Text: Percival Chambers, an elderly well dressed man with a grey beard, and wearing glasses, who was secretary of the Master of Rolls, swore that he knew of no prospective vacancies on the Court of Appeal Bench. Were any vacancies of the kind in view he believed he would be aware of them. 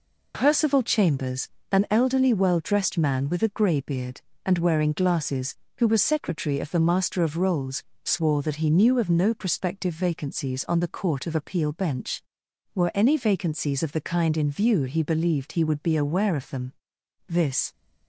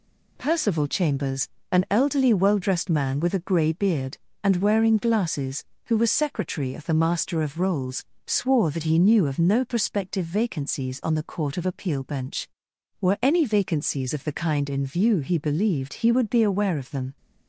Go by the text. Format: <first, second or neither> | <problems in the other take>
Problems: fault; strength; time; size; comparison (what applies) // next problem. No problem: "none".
second | goes on to say "This"; slight; from 17.2 s on; 0.44 s long